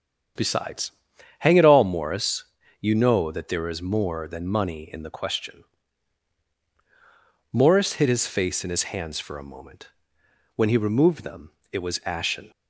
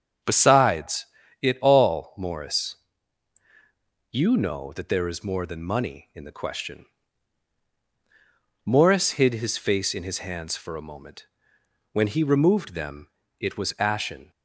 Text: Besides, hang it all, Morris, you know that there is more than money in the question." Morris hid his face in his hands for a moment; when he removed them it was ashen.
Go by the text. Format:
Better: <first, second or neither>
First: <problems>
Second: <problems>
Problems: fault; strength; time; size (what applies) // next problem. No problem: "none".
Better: first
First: starts louder than the rest; strong; until 1.8 s; 8.5 dB // pauses between "them" and "it"; slight; at 11.5 s; 0.20 s long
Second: starts louder than the rest; strong; until 1.5 s; 7.5 dB // skips "hang"; at 1.2 s // pauses between "them" and "it"; slight; at 13.0 s; 0.32 s long